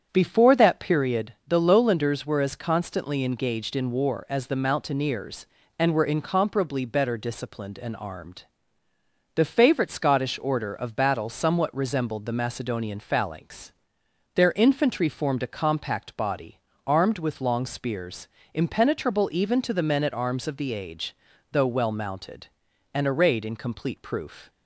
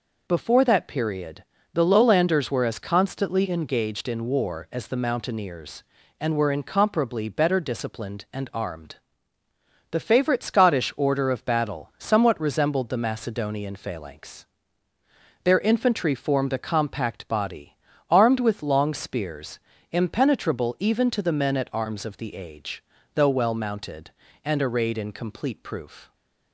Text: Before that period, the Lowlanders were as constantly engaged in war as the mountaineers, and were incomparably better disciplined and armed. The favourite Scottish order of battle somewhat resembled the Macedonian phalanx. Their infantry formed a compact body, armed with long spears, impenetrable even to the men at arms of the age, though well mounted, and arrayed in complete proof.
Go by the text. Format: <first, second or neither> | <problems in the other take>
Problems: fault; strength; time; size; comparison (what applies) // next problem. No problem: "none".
second | starts louder than the rest; strong; until 1.1 s; 8 dB